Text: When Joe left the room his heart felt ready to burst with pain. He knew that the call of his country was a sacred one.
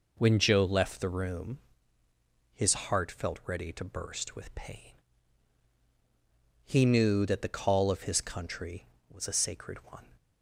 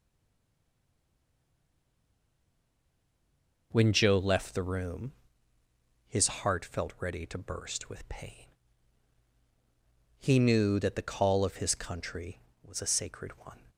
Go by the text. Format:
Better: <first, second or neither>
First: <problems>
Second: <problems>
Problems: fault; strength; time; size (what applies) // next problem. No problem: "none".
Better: first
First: pauses between "room" and "his"; noticeable; at 1.5 s; 0.92 s long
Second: stays silent before the first word; strong; until 3.7 s; 3.7 s long // pauses between "room" and "his"; noticeable; at 5.1 s; 0.92 s long